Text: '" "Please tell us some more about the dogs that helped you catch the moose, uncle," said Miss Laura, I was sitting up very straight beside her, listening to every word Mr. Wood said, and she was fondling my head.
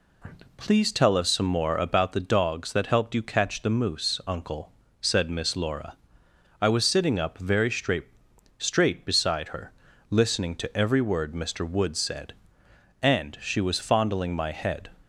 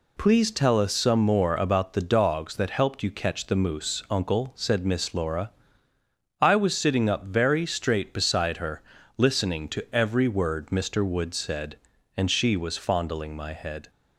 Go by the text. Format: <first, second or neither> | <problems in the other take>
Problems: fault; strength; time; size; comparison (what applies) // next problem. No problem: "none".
second | says "straight" twice; at 8.5 s